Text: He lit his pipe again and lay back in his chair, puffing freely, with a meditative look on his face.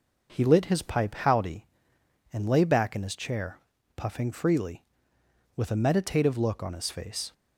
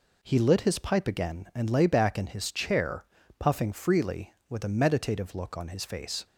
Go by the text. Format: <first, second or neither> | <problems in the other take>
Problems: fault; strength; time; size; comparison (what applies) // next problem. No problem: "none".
second | says "howdy" for "again"; at 1.1 s